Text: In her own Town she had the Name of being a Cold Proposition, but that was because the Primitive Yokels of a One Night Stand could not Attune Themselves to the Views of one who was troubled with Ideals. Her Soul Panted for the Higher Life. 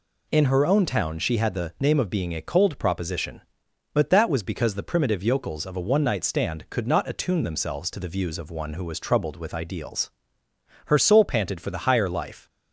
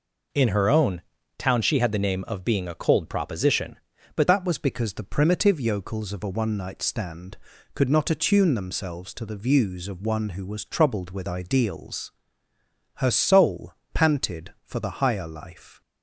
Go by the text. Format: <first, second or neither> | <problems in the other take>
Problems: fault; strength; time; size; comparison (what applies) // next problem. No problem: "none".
first | pauses between "own" and "Town"; slight; at 1.0 s; 0.36 s long // changes voice at "that"; from 4.2 s on; 11.6 s long // pauses between "Soul" and "Panted"; slight; at 13.7 s; 0.22 s long